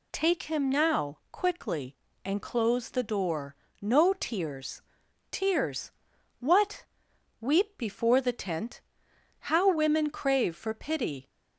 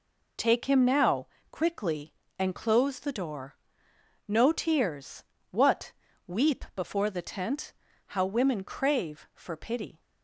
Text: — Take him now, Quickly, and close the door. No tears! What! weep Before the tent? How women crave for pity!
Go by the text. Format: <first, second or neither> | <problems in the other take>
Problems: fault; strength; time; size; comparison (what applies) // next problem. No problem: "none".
second | says "tears" twice; at 5.3 s